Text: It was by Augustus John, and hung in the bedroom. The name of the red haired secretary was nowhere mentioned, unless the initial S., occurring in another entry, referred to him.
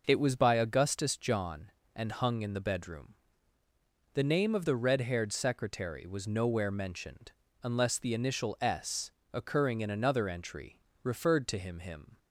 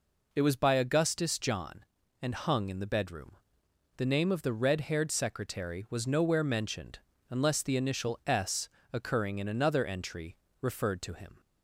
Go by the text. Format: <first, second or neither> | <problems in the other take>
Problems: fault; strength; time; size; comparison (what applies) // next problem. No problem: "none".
second | says "him" twice; at 11.7 s